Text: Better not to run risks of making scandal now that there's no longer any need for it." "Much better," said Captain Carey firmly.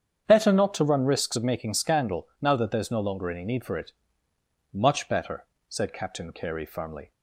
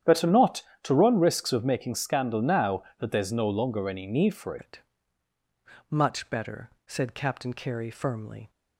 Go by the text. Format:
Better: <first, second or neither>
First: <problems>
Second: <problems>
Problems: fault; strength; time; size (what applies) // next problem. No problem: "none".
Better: first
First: starts louder than the rest; strong; until 1.2 s; 8 dB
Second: starts louder than the rest; strong; until 1.2 s; 9.5 dB // changes voice at "it"; from 4.5 s on; 3.9 s long